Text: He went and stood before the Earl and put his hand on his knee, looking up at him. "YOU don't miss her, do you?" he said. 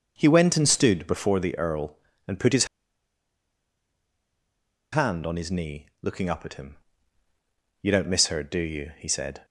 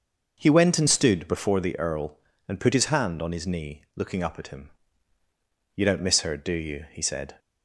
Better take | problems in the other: second | starts louder than the rest; until 1.1 s; 6 dB; also in the second // pauses between "his" and "hand"; strong; at 2.6 s; 2.2 s long

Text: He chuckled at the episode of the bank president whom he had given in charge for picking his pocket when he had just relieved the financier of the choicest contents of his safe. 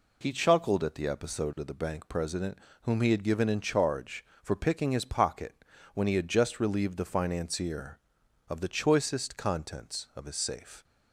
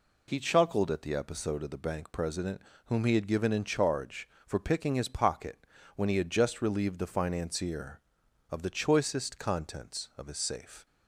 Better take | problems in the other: neither | pauses between "president" and "whom"; slight; the same in both // pauses between "pocket" and "when"; slight; the same in both

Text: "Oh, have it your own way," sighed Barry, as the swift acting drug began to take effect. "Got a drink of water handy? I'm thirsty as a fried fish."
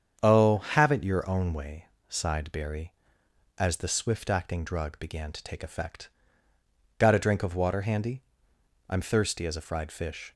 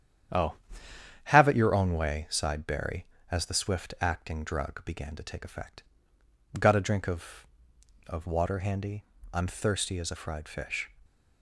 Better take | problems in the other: first | starts louder than the rest; strong; until 2.0 s; 9.5 dB; strong in the first // says "of" twice; at 8.0 s

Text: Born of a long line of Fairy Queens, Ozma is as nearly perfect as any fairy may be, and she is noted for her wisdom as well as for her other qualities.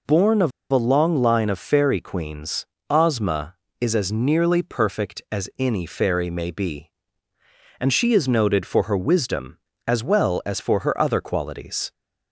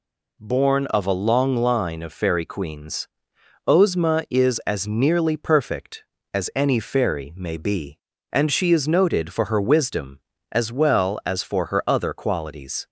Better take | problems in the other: second | pauses between "of" and "a"; slight; at 0.5 s; 0.20 s long

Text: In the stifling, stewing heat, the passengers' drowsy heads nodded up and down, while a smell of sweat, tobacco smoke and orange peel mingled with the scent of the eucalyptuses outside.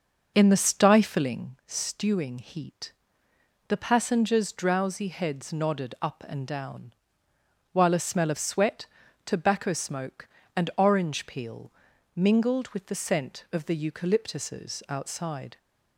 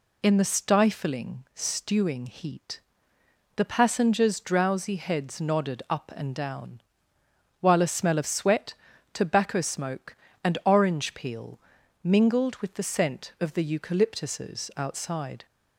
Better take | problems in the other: second | starts louder than the rest; noticeable; until 1.4 s; 5.5 dB // pauses between "peel" and "mingled"; at 11.7 s; 0.44 s long; also in the second

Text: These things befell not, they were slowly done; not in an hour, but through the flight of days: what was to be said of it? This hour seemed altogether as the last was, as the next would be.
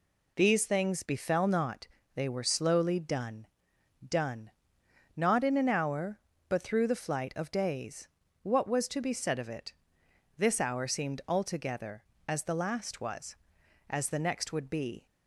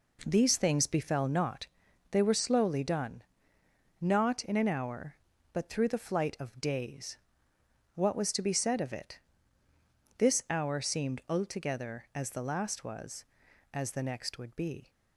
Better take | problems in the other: second | says "done" twice; at 4.0 s

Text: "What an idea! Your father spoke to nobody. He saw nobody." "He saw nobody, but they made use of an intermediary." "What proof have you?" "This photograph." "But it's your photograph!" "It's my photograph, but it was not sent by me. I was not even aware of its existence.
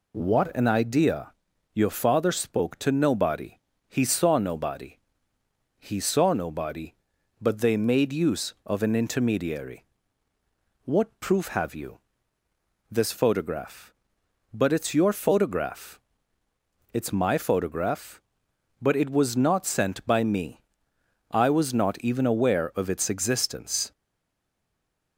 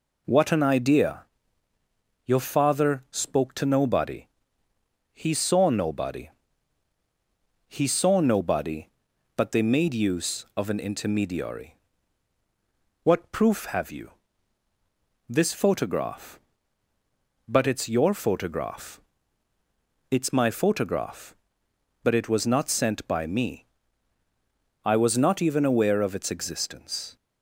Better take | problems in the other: second | stays silent after the last word; noticeable; from 23.9 s on; 1.2 s long

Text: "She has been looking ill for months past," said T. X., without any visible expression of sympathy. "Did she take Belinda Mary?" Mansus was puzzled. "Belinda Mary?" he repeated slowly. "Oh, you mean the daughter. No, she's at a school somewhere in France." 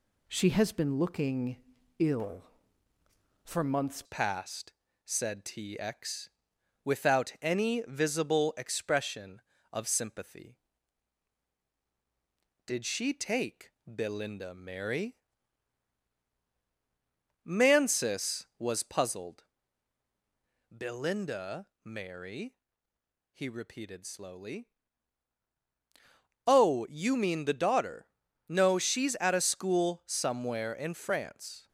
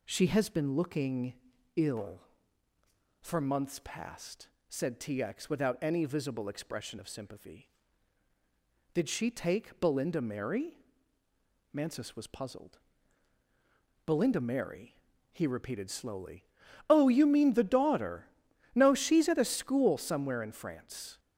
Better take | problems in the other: second | pauses between "looking" and "ill"; at 1.5 s; 0.42 s long; also in the second // changes voice at "past"; from 4.0 s on; 27.6 s long // pauses between "take" and "Belinda"; slight; at 13.6 s; 0.16 s long // pauses between "Belinda" and "Mary"; slight; at 21.6 s; 0.16 s long

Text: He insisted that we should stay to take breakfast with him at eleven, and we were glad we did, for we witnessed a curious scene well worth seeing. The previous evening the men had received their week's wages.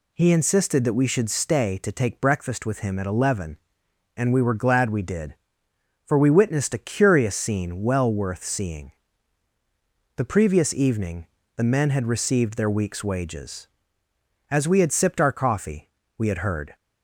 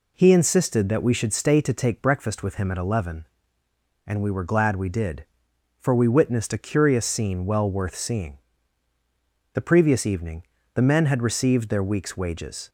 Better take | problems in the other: second | pauses between "evening" and "the"; slight; at 11.2 s; 0.30 s long; slight in the second // goes on to say "As we had sipped our coffee we had heard"; strong; from 14.5 s on; 2.2 s long

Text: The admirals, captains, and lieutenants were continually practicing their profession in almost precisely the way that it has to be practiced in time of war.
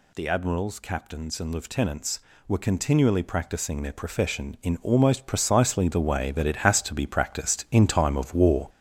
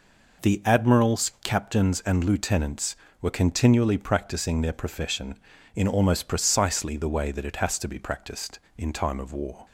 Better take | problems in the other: second | gets louder; throughout; 6.5 dB

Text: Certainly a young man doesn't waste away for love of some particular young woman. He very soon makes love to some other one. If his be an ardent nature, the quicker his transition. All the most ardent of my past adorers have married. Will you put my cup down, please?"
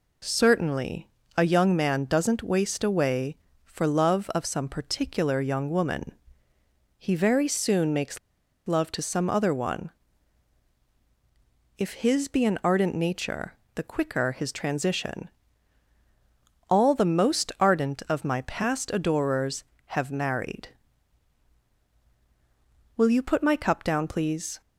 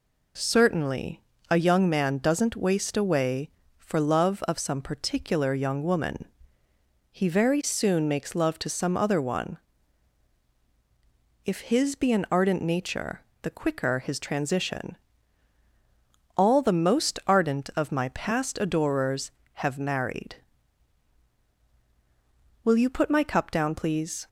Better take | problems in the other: second | pauses between "Certainly" and "a"; slight; at 1.0 s; 0.26 s long; slight in the second // pauses between "makes" and "love"; noticeable; at 8.1 s; 0.49 s long

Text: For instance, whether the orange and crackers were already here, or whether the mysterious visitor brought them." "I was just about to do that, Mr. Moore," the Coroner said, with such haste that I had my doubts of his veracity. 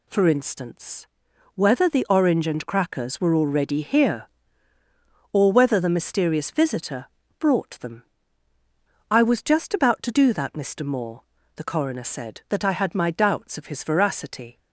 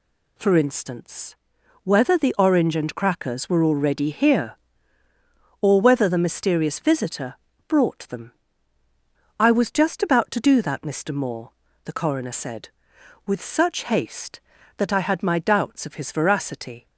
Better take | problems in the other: second | pauses between "visitor" and "brought"; slight; at 7.0 s; 0.32 s long; slight in the second // skips "with such haste"; at 12.4 s

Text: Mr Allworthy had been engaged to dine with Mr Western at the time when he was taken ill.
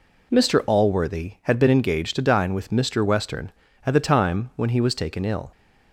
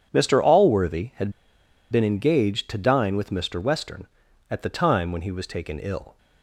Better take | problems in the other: first | pauses between "had" and "been"; noticeable; at 1.3 s; 0.60 s long

